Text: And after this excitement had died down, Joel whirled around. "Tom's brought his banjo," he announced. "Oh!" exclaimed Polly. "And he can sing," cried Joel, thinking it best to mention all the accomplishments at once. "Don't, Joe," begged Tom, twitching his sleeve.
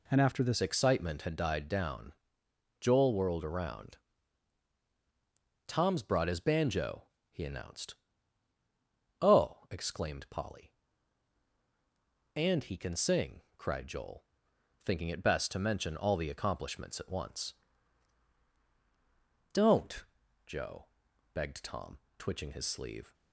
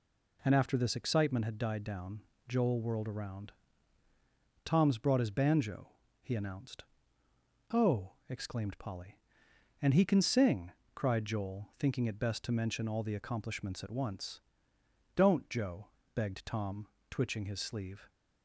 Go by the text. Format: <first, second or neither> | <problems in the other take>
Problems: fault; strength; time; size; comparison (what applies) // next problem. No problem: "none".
second | changes voice at "excitement"; from 0.6 s on; 22.5 s long